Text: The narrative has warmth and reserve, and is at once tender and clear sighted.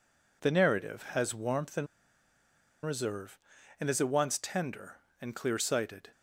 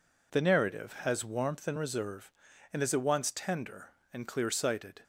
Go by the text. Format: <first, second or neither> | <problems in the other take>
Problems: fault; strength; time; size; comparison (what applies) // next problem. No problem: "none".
second | pauses between "and" and "reserve"; at 1.8 s; 0.99 s long